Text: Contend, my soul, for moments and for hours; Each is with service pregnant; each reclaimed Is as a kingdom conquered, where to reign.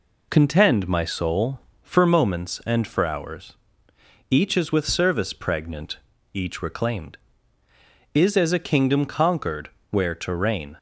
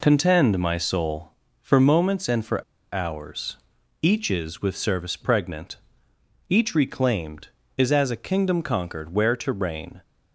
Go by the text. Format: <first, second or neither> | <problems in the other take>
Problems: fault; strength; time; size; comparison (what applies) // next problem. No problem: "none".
first | pauses between "for" and "hours"; slight; at 2.6 s; 0.29 s long